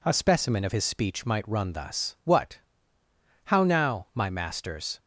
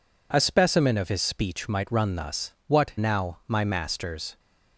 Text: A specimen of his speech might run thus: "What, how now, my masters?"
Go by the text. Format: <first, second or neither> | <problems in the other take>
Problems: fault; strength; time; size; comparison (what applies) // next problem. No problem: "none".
first | skips "how"; at 2.9 s